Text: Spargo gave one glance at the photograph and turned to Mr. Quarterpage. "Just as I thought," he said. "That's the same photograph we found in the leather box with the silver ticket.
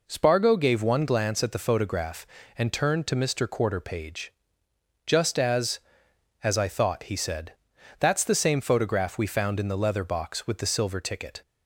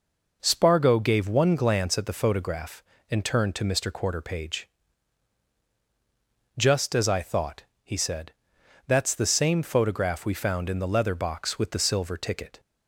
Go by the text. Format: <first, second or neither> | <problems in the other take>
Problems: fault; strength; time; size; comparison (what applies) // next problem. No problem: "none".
second | says "as" twice; at 6.4 s